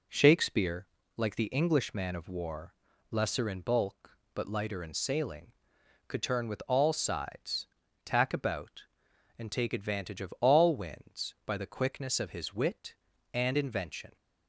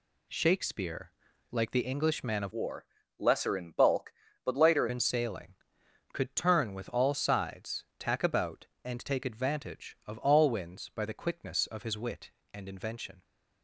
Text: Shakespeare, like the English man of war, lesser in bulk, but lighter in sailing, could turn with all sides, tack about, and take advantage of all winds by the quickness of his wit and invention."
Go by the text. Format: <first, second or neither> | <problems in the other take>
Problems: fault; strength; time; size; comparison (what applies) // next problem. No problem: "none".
first | changes voice from "war" to "lighter"; from 2.5 to 4.8 s; 2.3 s long